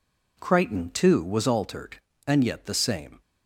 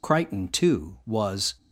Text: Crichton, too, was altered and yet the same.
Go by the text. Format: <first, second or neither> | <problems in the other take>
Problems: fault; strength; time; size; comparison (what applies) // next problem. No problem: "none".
first | stops before "altered and yet the same"; at 1.5 s